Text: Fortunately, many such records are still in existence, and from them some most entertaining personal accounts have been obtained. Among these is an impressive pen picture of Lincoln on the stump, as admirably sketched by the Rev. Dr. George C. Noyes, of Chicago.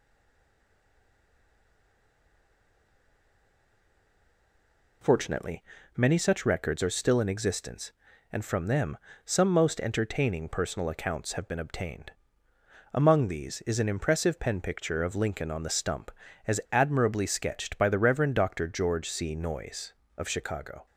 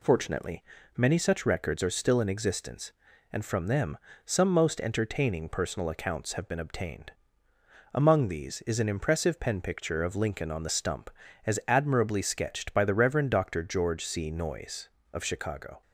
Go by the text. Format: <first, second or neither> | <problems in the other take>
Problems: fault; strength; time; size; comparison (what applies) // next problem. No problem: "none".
second | stays silent before the first word; strong; until 5.0 s; 5.0 s long // pauses between "them" and "some"; slight; at 8.9 s; 0.28 s long; slight in the second